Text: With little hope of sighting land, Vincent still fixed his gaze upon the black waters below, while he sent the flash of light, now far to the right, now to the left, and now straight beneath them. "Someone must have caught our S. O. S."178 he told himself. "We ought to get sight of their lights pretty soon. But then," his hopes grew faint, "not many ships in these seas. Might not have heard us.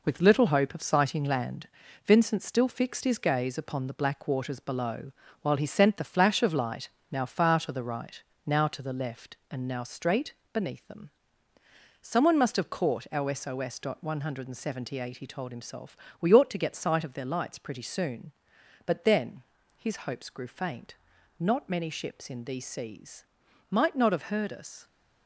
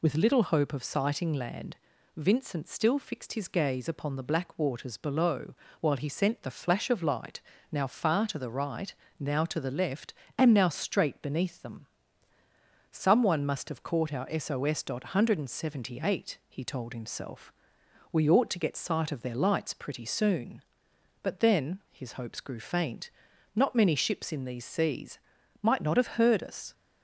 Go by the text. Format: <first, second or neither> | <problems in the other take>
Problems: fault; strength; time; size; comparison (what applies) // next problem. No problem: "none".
second | gets quieter; throughout; 6.5 dB // pauses between "straight" and "beneath"; slight; at 10.3 s; 0.22 s long